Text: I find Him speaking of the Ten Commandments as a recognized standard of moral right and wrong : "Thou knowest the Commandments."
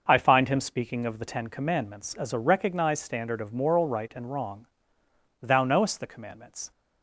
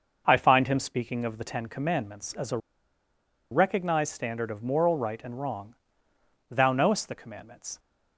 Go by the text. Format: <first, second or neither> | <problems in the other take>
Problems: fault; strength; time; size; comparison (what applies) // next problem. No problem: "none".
first | pauses between "a" and "recognized"; noticeable; at 2.5 s; 0.93 s long